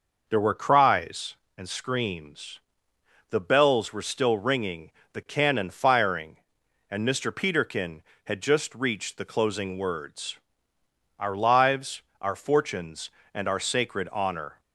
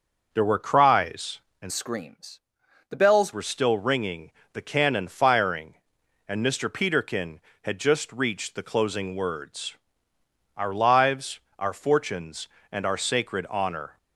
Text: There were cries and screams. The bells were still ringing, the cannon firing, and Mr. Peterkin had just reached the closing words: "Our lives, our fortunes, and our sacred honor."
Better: first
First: none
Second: starts louder than the rest; noticeable; until 1.3 s; 6 dB // changes voice from "screams" to "bells"; from 1.7 to 3.3 s; 1.6 s long

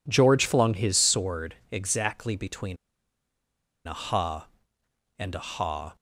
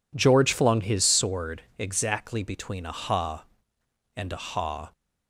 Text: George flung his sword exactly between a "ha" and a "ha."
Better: second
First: pauses between "sword" and "exactly"; slight; at 1.5 s; 0.16 s long // pauses between "between" and "a"; at 2.7 s; 1.1 s long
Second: pauses between "sword" and "exactly"; slight; at 1.6 s; 0.16 s long

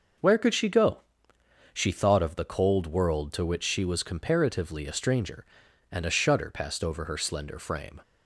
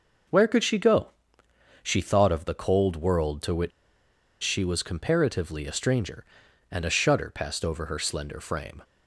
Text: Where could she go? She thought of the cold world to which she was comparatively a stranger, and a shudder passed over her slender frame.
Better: first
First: none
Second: pauses between "which" and "she"; noticeable; at 3.7 s; 0.72 s long

